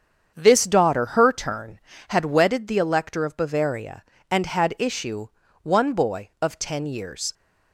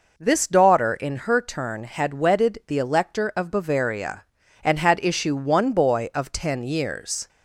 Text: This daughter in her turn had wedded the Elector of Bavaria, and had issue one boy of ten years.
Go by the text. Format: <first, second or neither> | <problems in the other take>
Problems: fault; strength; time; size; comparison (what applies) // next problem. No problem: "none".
second | starts louder than the rest; strong; until 1.3 s; 7.5 dB // skips "in"; at 1.0 s // pauses between "issue" and "one"; slight; at 5.2 s; 0.34 s long